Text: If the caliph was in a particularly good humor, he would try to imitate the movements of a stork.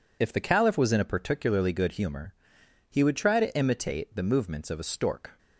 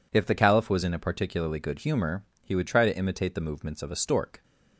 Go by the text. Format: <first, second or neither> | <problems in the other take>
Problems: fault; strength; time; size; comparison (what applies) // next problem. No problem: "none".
neither | none